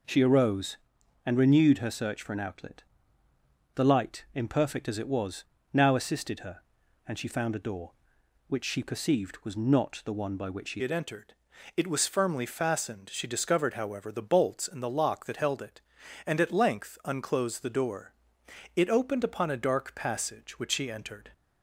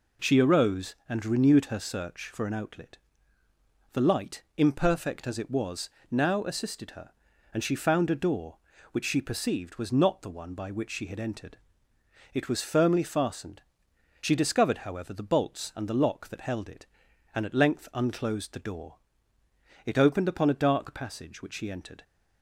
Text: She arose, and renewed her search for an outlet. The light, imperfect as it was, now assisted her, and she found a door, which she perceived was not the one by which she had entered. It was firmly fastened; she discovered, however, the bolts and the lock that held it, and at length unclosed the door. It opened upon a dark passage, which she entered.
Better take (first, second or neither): second